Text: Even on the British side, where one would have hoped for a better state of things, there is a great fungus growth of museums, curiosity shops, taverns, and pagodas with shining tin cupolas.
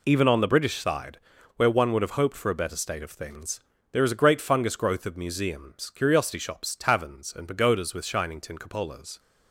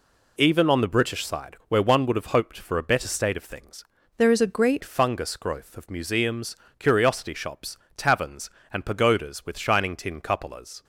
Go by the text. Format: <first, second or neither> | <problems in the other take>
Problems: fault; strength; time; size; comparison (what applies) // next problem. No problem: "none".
first | changes voice from "there" to "great"; from 4.1 to 4.8 s; 0.7 s long